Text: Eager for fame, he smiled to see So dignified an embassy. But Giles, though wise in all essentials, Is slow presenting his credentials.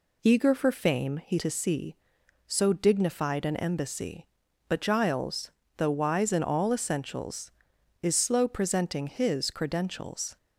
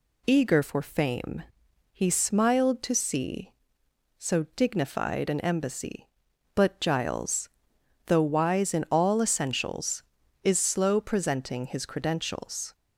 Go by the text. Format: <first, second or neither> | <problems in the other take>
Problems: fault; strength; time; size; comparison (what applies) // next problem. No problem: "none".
second | skips "smiled"; at 1.3 s